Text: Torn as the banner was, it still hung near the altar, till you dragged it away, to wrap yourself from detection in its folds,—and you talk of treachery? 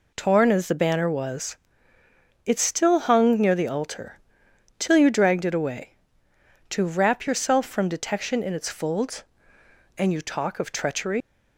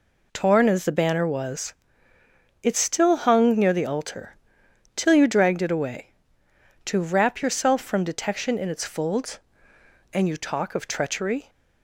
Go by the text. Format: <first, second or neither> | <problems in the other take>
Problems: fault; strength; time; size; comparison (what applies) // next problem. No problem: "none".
second | leaves "treachery" unfinished; at 11.2 s; 135 ms